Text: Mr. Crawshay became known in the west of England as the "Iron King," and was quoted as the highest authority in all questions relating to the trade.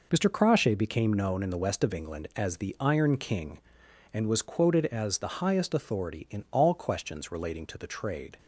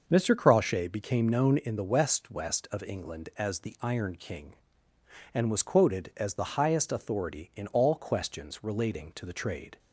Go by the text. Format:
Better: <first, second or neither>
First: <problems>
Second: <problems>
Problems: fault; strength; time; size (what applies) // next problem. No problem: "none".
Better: first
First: none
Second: starts louder than the rest; noticeable; until 1.0 s; 6 dB // says "west" twice; at 2.3 s